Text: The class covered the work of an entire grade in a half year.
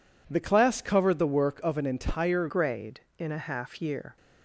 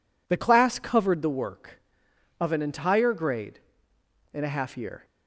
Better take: second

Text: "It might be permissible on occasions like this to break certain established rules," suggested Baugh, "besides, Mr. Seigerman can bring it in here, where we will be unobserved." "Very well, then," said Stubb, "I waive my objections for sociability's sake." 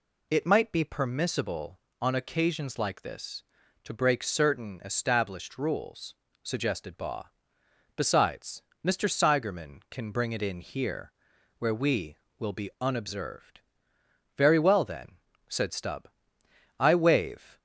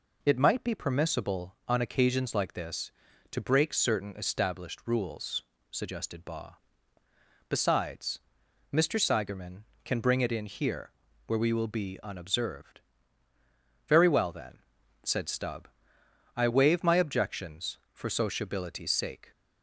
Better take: second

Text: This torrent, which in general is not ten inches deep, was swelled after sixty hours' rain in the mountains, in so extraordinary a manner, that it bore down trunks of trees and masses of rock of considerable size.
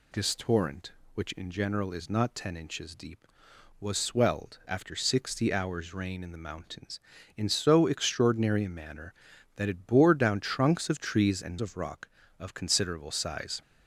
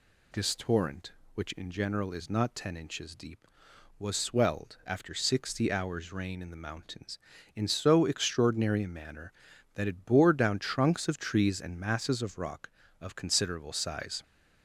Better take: second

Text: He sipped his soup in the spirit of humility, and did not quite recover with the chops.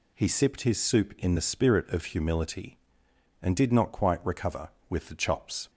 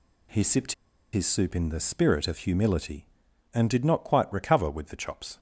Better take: first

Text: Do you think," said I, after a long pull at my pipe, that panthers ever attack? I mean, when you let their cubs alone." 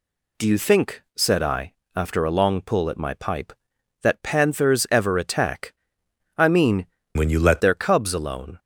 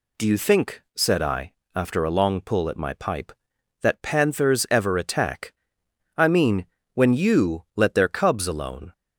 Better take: second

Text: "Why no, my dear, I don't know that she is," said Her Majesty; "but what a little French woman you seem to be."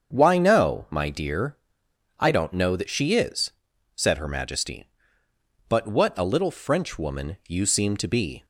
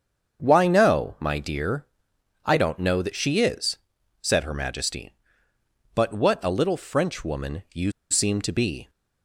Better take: first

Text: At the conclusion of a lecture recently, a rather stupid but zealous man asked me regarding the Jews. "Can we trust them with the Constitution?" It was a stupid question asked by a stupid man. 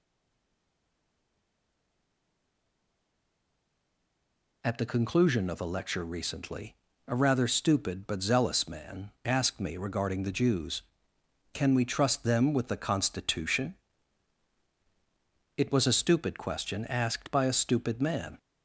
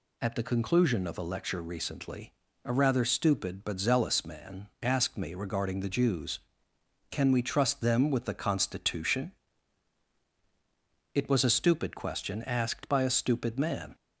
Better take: second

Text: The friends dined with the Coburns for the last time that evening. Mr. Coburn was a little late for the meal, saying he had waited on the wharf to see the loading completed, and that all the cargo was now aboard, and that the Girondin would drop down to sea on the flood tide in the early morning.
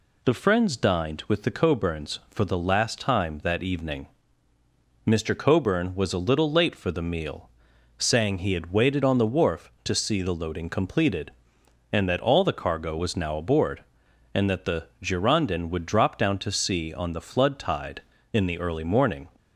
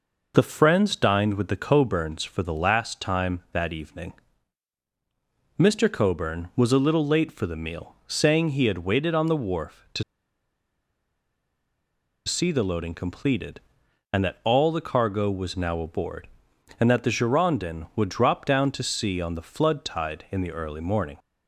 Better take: first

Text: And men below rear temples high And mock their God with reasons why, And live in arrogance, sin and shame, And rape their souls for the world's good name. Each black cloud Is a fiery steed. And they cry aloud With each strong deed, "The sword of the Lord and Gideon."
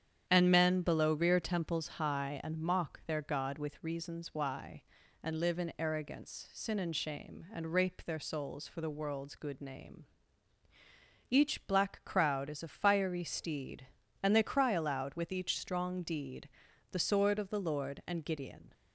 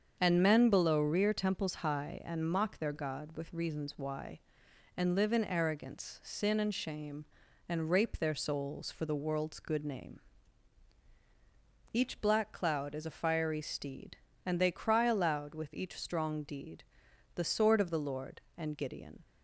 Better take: second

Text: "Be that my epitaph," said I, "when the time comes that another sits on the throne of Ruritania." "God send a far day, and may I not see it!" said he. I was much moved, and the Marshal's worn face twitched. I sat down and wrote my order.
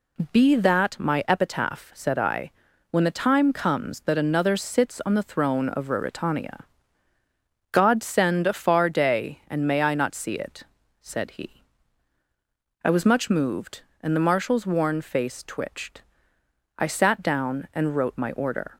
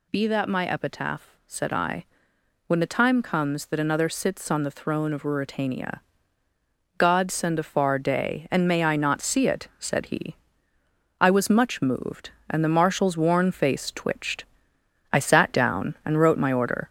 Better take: first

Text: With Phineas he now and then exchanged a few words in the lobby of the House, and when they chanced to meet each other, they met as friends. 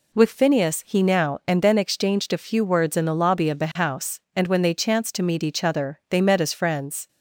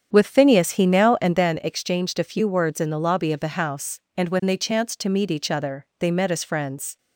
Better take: first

